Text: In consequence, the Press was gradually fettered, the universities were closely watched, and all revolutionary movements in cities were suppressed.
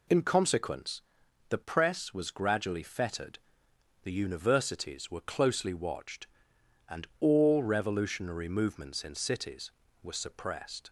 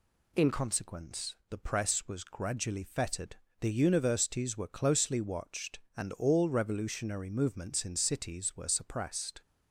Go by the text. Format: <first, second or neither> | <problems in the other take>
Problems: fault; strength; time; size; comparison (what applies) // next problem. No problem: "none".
first | changes voice at "consequence"; from 0.5 s on; 8.9 s long